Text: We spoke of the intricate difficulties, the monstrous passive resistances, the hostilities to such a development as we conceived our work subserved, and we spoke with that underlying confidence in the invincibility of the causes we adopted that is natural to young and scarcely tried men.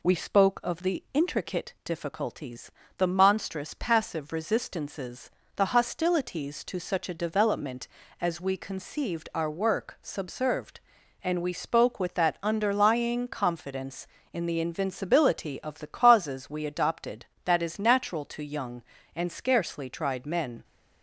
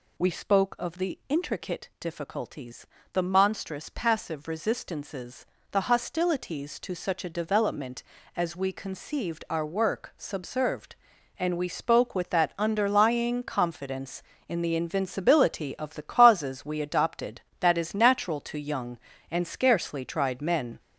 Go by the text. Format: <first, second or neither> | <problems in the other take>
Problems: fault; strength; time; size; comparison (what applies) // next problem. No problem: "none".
first | gets louder; noticeable; throughout; 5 dB